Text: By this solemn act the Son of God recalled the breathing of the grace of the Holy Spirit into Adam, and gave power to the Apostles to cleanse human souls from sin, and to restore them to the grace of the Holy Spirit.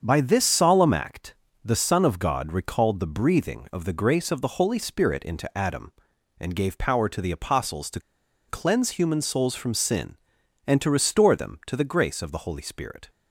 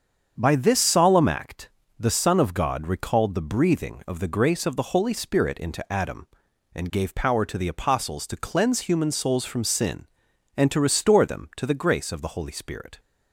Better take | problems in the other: second | starts louder than the rest; strong; until 1.0 s; 7 dB; strong in the second // pauses between "act" and "the"; slight; at 1.3 s; 0.28 s long; slight in the second // pauses between "to" and "cleanse"; noticeable; at 7.9 s; 0.49 s long

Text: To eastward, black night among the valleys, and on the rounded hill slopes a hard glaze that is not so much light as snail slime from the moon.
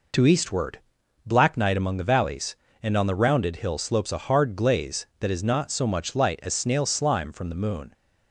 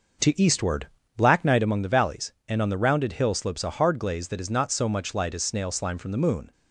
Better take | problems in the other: first | starts louder than the rest; noticeable; until 1.7 s; 6 dB

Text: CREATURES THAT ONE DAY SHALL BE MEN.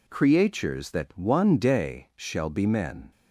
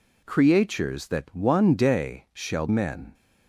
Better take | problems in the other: first | skips "BE"; at 2.6 s

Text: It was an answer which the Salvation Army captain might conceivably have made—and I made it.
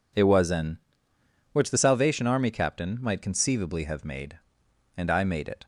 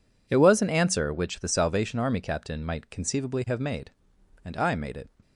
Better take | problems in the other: second | skips "answer"; at 1.1 s

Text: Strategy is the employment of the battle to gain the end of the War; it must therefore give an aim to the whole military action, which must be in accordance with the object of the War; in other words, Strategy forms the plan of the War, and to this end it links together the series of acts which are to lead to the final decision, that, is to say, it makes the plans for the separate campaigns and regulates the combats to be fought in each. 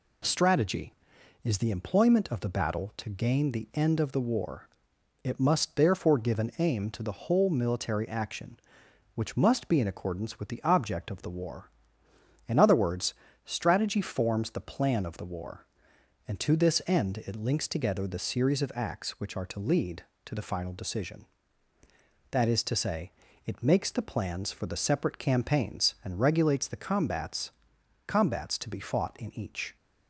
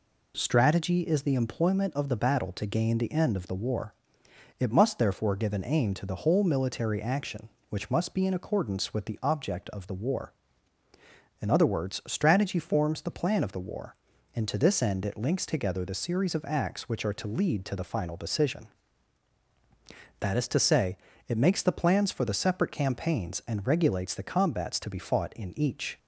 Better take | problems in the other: second | says "combats" twice; at 28.0 s

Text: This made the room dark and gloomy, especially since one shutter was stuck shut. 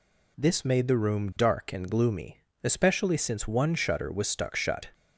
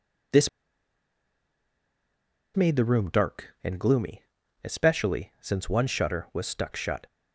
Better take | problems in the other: first | pauses between "This" and "made"; strong; at 0.4 s; 2.0 s long

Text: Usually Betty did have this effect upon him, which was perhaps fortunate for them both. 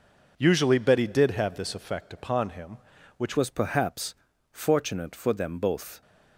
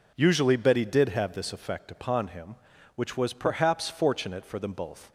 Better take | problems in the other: second | changes voice at "was"; from 3.3 s on; 2.7 s long // pauses between "perhaps" and "fortunate"; at 4.1 s; 0.38 s long

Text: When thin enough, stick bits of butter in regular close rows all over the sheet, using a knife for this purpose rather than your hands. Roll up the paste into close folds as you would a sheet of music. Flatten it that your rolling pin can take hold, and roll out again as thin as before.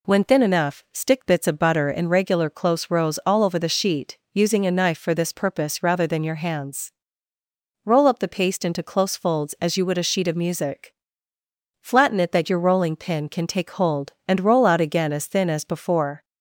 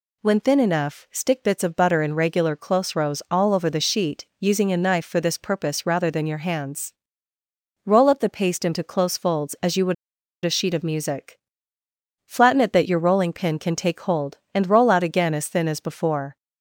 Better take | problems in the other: first | pauses between "would" and "a"; noticeable; at 9.9 s; 0.49 s long

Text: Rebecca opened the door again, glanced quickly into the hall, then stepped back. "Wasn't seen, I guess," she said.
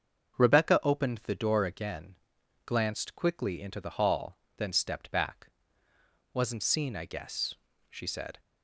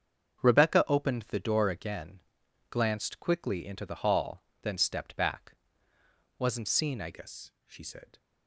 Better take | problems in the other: first | starts louder than the rest; strong; until 1.4 s; 7 dB; also in the first // changes voice at "guess"; from 7.1 s on; 1.0 s long

